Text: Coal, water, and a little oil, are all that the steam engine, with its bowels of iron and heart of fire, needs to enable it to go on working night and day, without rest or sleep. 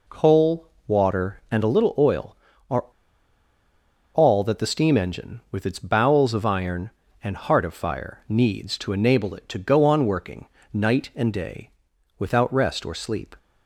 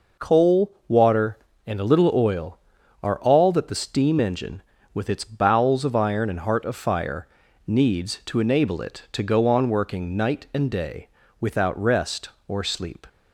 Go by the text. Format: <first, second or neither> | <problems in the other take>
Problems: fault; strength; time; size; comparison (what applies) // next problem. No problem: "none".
second | pauses between "are" and "all"; strong; at 2.8 s; 1.2 s long // pauses between "working" and "night"; slight; at 10.4 s; 0.26 s long